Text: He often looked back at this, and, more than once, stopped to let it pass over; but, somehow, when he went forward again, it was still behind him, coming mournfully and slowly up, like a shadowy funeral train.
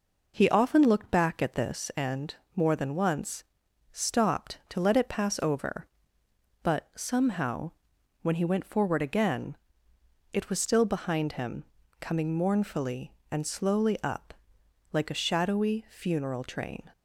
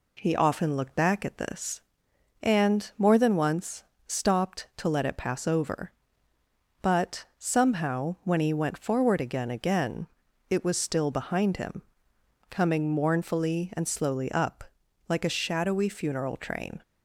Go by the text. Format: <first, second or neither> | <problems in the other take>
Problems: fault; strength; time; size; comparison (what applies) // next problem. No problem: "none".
first | says "again" twice; at 9.5 s